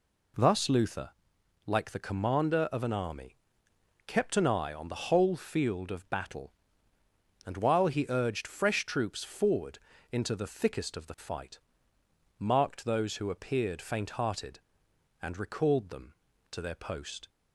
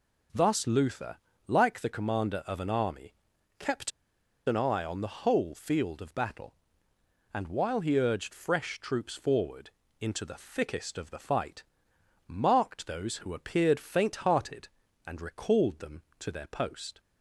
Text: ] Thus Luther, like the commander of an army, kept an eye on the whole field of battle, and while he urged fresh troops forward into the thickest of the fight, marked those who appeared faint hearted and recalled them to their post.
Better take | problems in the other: first | pauses between "kept" and "an"; noticeable; at 3.9 s; 0.56 s long // pauses between "forward" and "into"; slight; at 9.7 s; 0.28 s long; slight in the first

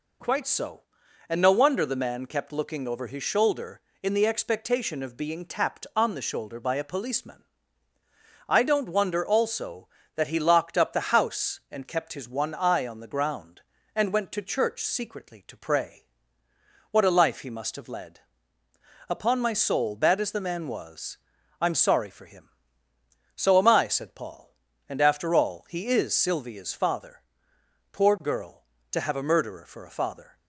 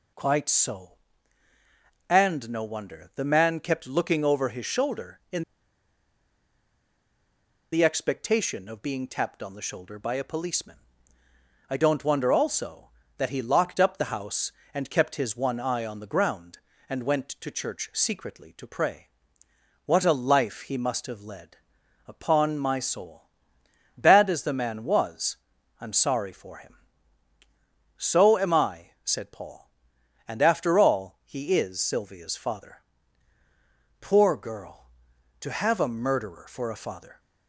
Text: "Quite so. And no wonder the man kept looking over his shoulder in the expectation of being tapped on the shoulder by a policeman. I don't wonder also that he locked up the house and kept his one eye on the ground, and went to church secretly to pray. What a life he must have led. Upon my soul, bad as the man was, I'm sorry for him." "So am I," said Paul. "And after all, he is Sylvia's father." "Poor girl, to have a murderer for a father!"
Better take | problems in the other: first | pauses between "in" and "the"; strong; at 5.4 s; 2.2 s long

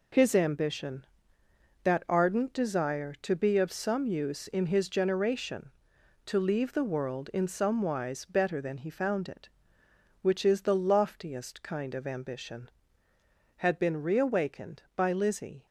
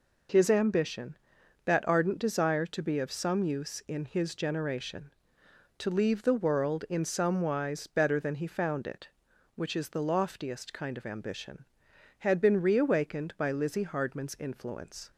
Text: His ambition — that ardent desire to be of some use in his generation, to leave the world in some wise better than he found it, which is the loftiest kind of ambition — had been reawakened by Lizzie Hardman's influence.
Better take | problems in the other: second | stops before "Hardman's influence"; at 15.6 s

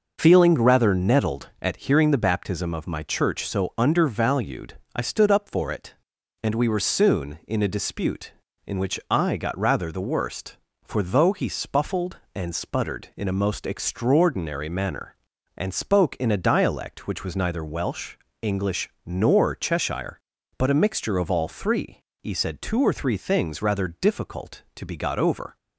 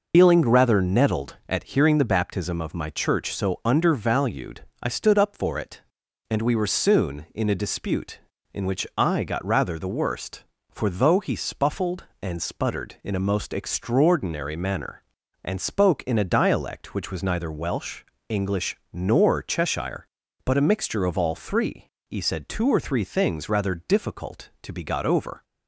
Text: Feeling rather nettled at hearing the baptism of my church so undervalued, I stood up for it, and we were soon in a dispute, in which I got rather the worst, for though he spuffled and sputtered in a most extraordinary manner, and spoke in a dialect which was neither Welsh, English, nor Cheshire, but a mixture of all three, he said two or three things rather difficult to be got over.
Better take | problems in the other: first | loses the start of "Feeling"; at 0.1 s; 95 ms

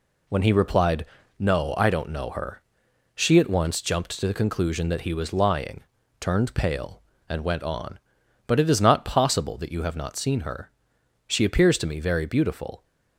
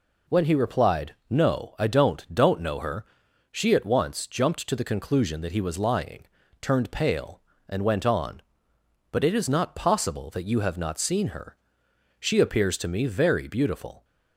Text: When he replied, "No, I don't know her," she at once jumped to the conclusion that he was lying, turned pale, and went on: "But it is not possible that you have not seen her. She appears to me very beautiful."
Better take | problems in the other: first | says "don't" twice; at 2.3 s

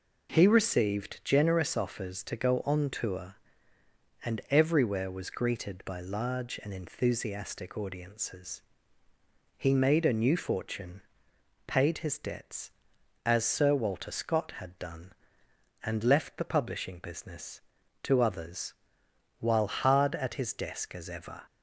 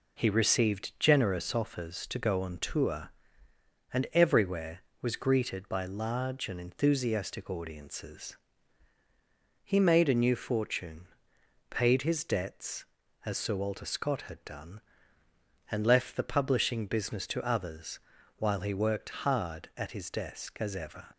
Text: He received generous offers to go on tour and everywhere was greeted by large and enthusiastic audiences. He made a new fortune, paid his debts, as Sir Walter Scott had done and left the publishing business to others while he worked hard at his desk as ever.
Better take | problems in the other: second | pauses between "others" and "while"; noticeable; at 18.7 s; 0.68 s long; also in the second // skips "he worked"; at 19.6 s

